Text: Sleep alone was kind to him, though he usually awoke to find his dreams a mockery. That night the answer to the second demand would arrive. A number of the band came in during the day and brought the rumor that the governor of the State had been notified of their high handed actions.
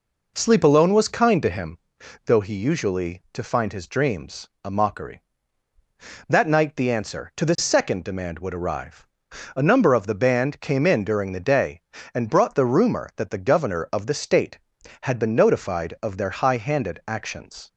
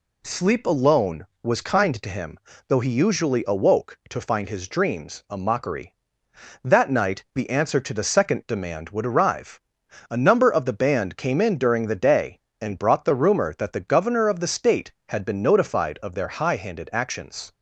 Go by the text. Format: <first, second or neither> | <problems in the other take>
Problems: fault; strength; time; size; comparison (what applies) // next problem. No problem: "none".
second | skips "awoke"; at 3.2 s // pauses between "dreams" and "a"; slight; at 4.4 s; 0.16 s long